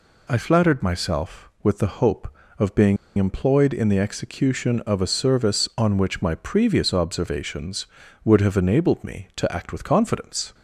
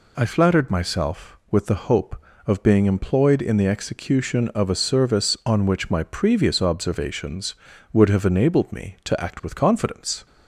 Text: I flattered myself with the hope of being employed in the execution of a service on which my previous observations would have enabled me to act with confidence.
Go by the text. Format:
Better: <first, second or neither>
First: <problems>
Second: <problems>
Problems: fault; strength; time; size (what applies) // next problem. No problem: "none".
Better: second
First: pauses between "being" and "employed"; slight; at 2.9 s; 0.21 s long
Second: none